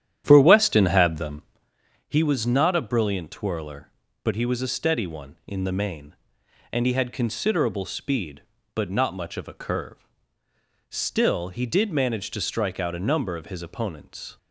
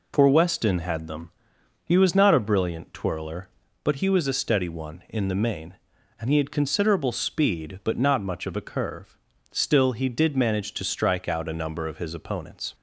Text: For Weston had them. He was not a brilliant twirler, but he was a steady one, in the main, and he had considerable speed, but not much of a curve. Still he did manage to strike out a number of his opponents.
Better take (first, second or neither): second